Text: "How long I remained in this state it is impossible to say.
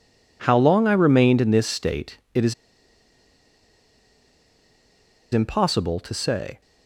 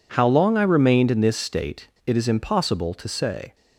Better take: second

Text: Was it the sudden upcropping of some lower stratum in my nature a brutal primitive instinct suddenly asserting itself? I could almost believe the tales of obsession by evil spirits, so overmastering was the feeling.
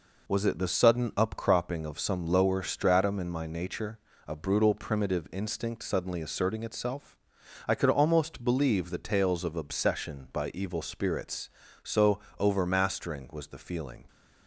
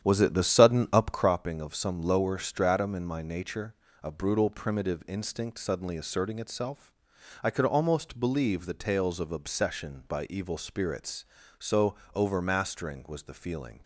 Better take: first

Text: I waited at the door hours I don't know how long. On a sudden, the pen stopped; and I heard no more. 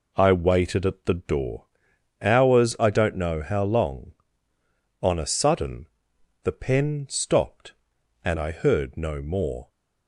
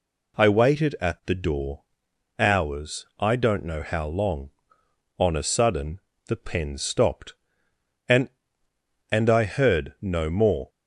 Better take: first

